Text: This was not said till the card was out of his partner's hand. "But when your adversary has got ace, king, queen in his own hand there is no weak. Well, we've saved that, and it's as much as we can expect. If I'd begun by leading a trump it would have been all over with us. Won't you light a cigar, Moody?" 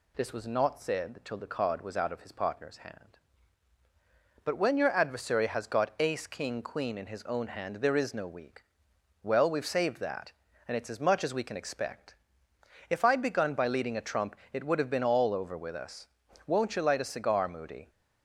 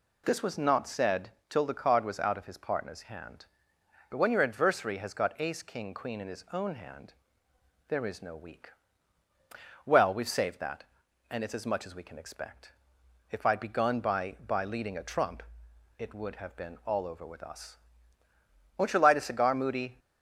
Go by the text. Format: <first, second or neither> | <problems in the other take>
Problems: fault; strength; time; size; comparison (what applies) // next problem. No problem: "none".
first | pauses between "said" and "till"; slight; at 1.2 s; 0.20 s long // pauses between "hand" and "there"; noticeable; at 7.1 s; 0.76 s long // says "by" twice; at 14.4 s // pauses between "trump" and "it"; noticeable; at 15.4 s; 0.56 s long; slight in the first